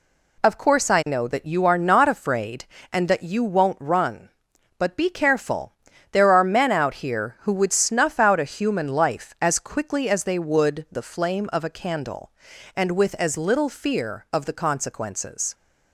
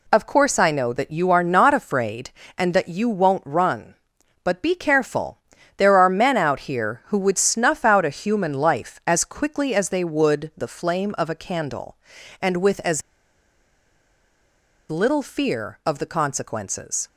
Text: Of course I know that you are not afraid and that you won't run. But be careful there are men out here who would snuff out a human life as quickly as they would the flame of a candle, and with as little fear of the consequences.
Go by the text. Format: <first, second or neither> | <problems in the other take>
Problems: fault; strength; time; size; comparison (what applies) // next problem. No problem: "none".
first | pauses between "careful" and "there"; at 5.3 s; 0.38 s long; also in the first // pauses between "as" and "little"; strong; at 13.0 s; 1.9 s long